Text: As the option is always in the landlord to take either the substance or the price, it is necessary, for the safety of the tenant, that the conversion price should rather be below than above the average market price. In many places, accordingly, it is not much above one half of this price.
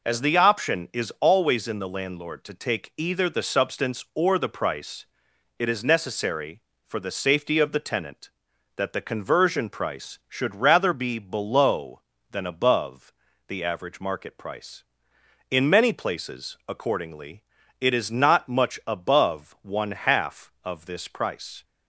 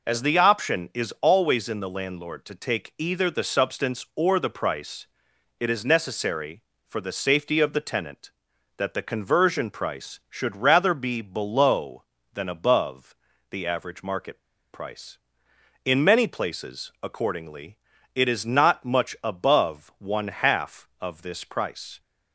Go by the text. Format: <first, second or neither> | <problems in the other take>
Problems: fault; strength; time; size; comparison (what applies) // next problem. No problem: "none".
first | pauses between "above" and "the"; slight; at 13.1 s; 0.36 s long; slight in the first // pauses between "market" and "price"; slight; at 14.3 s; 0.32 s long